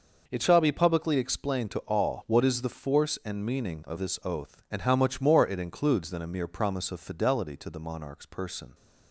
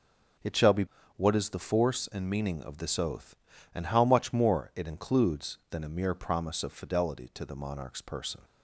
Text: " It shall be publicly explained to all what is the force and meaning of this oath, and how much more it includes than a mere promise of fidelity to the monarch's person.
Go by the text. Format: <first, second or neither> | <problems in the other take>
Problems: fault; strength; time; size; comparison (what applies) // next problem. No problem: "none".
first | skips "publicly explained to all"; at 1.0 s